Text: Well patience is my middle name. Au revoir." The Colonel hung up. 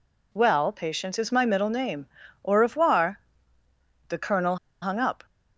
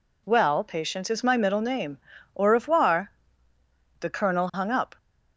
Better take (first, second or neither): second